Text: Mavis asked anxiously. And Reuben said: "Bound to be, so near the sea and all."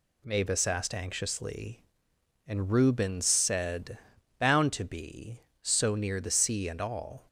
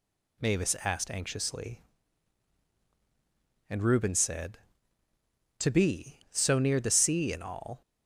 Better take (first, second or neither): first